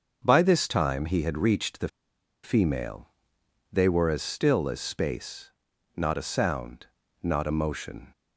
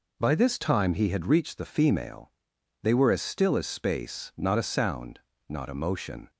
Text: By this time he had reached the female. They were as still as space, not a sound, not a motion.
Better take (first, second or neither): second